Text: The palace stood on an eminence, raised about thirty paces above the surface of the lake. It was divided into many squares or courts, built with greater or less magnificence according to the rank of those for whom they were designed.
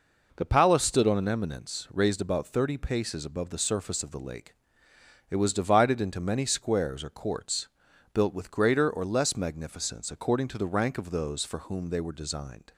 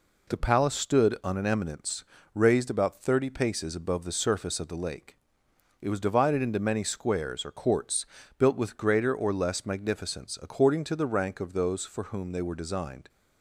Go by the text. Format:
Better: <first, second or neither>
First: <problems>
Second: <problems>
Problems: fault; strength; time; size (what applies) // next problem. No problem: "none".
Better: neither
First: none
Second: none